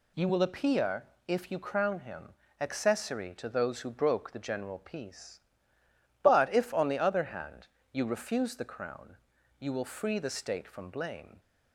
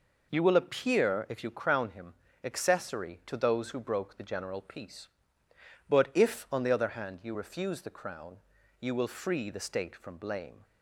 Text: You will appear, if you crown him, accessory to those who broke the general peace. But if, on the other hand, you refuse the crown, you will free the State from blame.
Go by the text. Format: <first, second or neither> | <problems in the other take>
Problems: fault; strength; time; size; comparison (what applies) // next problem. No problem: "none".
neither | none